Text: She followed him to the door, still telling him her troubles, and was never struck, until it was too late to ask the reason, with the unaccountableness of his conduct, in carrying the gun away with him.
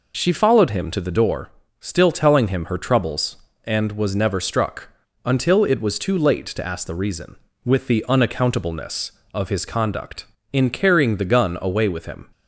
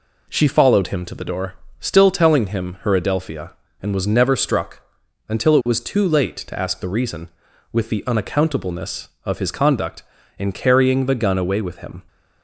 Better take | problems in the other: first | says "adelphia" for "troubles"; at 2.9 s

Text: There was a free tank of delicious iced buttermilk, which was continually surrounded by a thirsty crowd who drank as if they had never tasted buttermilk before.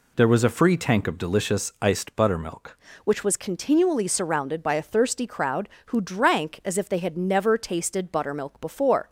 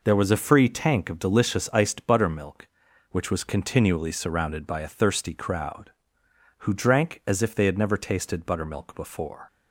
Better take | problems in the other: second | changes voice at "which"; from 3.0 s on; 6.0 s long

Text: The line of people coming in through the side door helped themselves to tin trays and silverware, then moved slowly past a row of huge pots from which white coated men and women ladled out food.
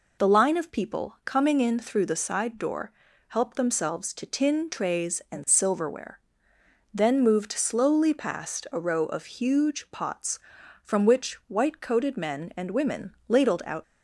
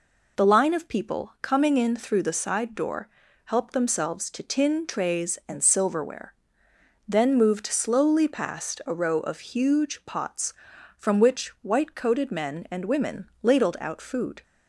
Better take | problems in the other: second | pauses between "door" and "helped"; at 2.9 s; 0.38 s long; also in the second // stops before "food"; at 13.8 s

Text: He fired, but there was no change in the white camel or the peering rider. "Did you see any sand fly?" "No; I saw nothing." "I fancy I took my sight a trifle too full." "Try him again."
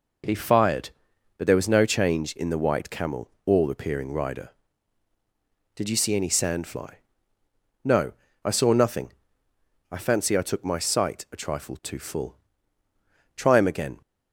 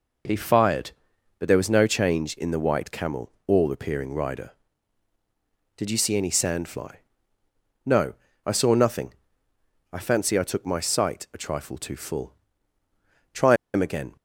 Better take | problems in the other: first | pauses between "Try" and "him"; slight; at 13.5 s; 0.19 s long

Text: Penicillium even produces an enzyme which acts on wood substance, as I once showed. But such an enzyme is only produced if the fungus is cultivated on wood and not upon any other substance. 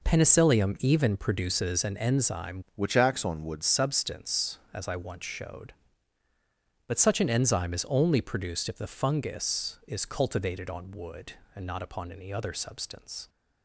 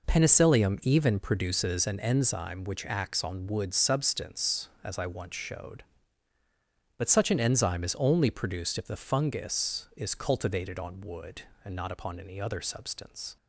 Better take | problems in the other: second | changes voice from "which" to "wood"; from 2.7 to 3.6 s; 0.9 s long

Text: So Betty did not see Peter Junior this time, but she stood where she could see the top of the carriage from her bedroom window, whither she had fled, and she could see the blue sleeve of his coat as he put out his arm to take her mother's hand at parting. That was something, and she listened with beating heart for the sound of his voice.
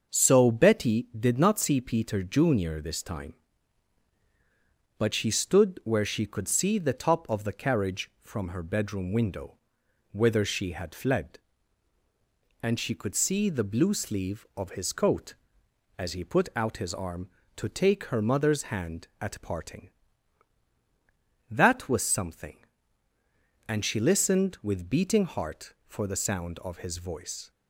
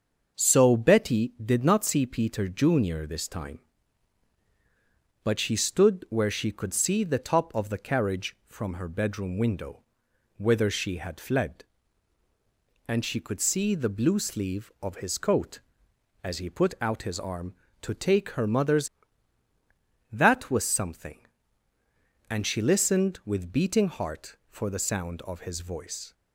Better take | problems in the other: first | starts louder than the rest; until 1.4 s; 6.5 dB; also in the first // skips "hand at parting"; at 19.5 s

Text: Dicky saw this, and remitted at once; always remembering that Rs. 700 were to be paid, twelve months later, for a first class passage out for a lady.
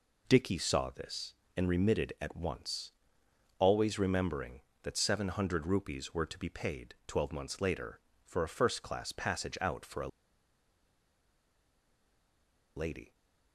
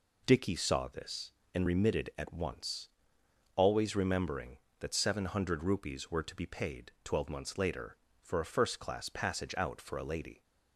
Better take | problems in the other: second | pauses between "a" and "lady"; strong; at 10.0 s; 2.6 s long

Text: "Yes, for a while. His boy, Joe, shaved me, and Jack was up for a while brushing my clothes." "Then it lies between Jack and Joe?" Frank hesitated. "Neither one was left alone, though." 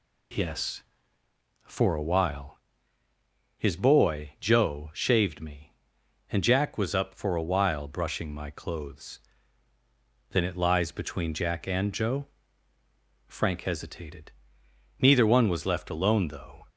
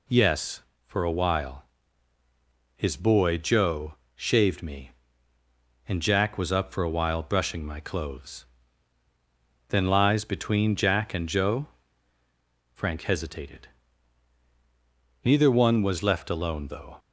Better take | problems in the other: first | skips "it"; at 9.8 s

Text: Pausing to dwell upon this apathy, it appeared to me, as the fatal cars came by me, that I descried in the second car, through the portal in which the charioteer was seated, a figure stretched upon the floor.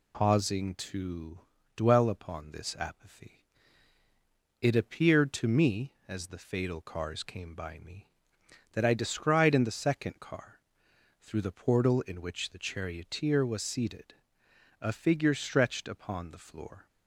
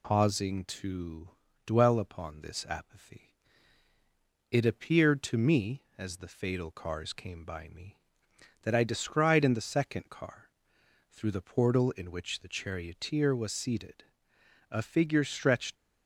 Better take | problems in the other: first | pauses between "to" and "dwell"; slight; at 1.2 s; 0.36 s long; slight in the first // stops before "upon the floor"; at 15.7 s

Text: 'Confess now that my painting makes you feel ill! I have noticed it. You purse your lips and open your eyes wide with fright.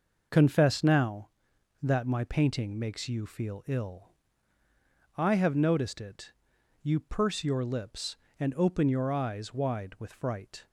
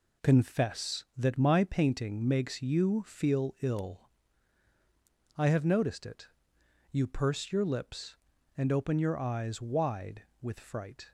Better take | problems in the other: first | skips "now"; at 1.1 s

